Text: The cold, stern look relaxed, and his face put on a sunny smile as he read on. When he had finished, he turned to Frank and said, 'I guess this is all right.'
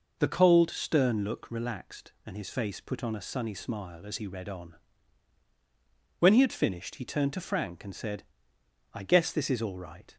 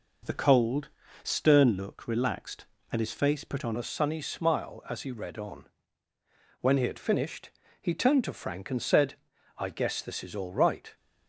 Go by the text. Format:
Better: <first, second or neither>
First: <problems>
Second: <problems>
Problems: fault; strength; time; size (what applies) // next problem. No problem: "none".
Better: first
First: none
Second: changes voice at "a"; from 3.7 s on; 7.2 s long